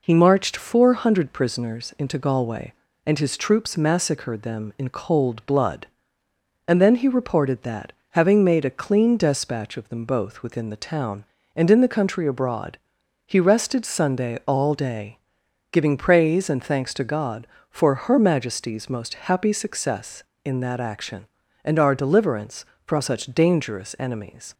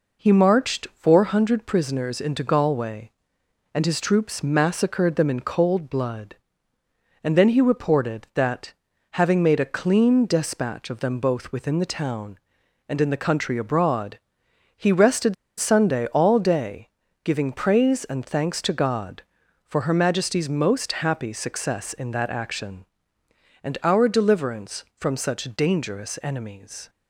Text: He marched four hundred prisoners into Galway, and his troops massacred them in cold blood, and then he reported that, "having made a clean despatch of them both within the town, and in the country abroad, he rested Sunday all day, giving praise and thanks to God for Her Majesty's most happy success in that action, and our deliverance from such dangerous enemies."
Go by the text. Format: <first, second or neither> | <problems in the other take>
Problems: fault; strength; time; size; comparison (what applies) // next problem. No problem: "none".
first | pauses between "rested" and "Sunday"; slight; at 15.3 s; 0.24 s long